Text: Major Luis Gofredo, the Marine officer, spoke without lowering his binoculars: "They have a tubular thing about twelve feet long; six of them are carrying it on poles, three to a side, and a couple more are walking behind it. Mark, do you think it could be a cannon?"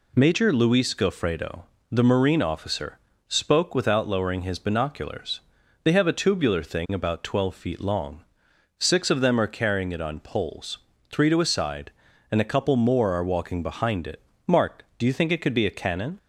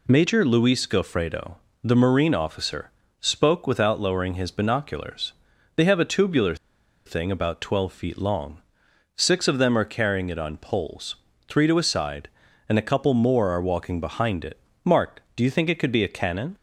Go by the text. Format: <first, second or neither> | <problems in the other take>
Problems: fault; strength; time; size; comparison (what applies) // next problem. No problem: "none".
first | pauses between "tubular" and "thing"; noticeable; at 6.5 s; 0.51 s long